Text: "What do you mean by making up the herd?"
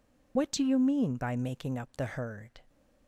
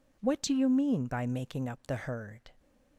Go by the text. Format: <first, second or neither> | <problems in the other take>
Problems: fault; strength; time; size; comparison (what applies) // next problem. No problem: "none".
second | loses the start of "What"; at 0.3 s; 55 ms